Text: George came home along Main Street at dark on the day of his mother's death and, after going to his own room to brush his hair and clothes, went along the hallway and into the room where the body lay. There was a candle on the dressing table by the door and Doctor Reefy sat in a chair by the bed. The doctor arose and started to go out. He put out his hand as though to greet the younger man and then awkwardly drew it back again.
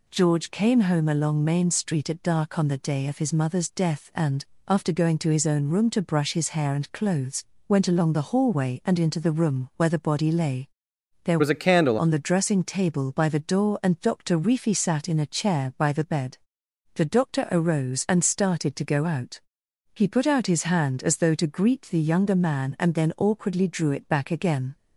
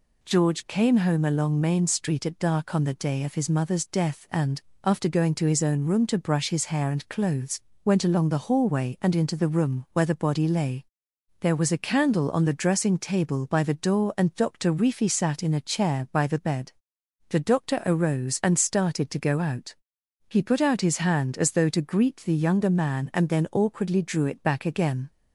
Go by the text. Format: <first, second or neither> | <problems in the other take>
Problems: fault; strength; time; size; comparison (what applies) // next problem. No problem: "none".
second | changes voice from "was" to "candle"; from 11.4 to 11.9 s; 0.5 s long